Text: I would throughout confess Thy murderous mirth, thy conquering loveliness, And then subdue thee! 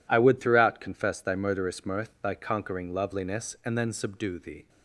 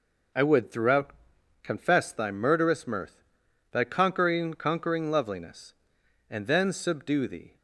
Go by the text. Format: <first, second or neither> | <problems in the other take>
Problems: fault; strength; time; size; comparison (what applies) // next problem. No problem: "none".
first | pauses between "throughout" and "confess"; noticeable; at 1.1 s; 0.52 s long // says "conquering" twice; at 4.5 s